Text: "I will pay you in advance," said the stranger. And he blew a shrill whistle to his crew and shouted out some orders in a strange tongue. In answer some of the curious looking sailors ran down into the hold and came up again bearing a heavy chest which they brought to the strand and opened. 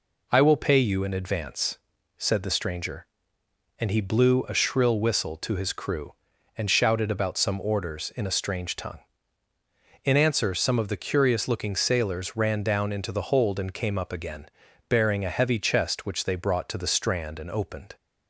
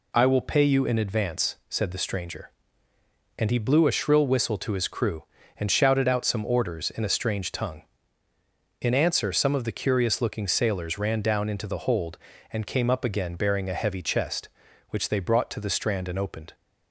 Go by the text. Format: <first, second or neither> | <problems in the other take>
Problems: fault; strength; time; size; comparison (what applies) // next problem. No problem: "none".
second | says "about" for "out"; at 7.0 s // pauses between "again" and "bearing"; at 14.4 s; 0.40 s long